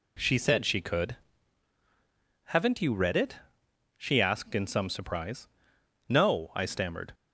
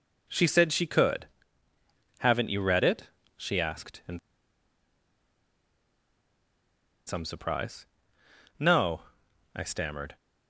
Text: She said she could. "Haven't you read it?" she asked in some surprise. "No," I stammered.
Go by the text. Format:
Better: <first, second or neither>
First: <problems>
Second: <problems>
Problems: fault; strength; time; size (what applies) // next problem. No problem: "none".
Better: first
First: none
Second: pauses between "in" and "some"; strong; at 4.1 s; 2.8 s long